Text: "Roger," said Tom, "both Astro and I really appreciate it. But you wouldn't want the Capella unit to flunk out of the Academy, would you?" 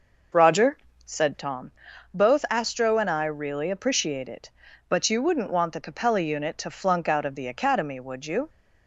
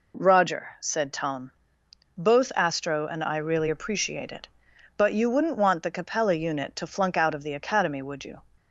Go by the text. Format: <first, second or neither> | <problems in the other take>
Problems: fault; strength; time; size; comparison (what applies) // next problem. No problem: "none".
second | starts louder than the rest; noticeable; until 1.5 s; 5.5 dB